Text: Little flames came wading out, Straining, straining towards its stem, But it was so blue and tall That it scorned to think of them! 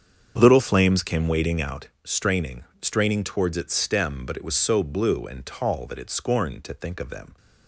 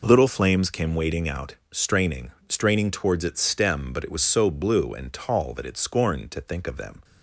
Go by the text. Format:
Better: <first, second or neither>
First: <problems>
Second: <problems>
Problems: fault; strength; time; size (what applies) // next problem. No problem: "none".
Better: second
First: starts louder than the rest; strong; until 1.8 s; 7.5 dB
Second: none